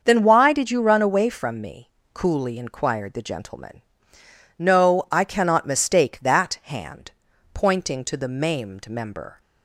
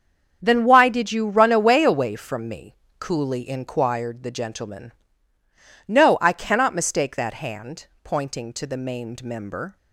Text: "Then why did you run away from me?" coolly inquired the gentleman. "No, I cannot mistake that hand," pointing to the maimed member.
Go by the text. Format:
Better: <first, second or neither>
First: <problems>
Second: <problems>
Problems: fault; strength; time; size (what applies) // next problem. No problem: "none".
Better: first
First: starts louder than the rest; until 1.0 s; 6.5 dB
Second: starts louder than the rest; strong; until 1.4 s; 7.5 dB // says "away" twice; at 1.8 s